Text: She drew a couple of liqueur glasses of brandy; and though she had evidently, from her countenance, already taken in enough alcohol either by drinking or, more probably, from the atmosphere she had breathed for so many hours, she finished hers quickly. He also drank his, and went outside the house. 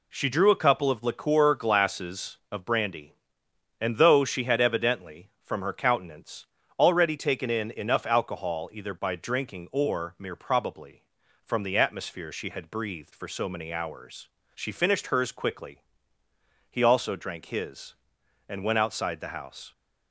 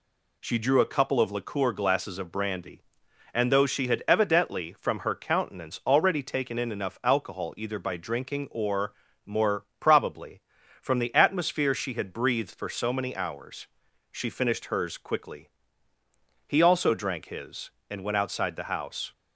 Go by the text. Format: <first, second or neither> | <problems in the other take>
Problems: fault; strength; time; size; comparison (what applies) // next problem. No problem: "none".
second | says "mere" for "more"; at 10.1 s